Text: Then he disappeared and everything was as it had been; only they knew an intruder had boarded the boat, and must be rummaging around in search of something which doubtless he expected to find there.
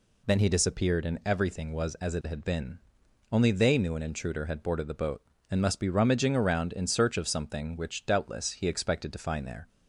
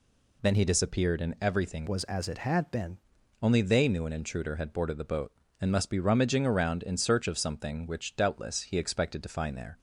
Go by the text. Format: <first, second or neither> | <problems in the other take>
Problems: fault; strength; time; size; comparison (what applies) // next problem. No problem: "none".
first | changes voice from "was" to "been"; from 1.8 to 2.9 s; 1.1 s long